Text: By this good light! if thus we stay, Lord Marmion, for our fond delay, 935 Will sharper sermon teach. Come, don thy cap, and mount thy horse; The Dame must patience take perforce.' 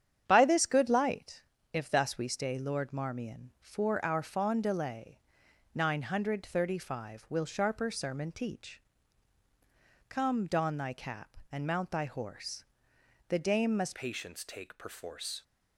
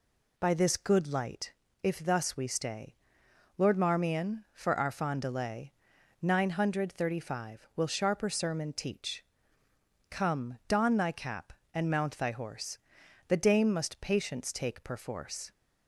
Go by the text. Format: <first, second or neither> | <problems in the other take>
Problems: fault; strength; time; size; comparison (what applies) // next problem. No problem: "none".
second | starts louder than the rest; strong; until 1.2 s; 9 dB // changes voice at "patience"; from 13.9 s on; 1.5 s long